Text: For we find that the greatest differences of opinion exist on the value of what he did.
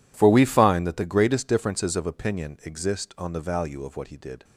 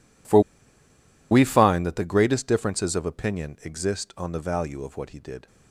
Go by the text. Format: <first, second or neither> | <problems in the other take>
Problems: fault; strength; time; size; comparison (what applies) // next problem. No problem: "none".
first | pauses between "For" and "we"; noticeable; at 0.3 s; 0.91 s long